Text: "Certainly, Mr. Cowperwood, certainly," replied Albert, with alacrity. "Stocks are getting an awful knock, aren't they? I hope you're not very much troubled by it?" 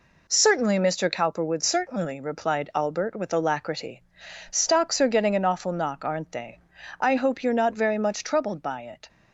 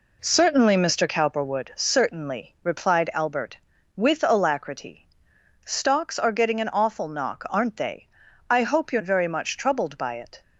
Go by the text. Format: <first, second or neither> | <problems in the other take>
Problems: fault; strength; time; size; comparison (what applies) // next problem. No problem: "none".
first | skips "not"; at 9.0 s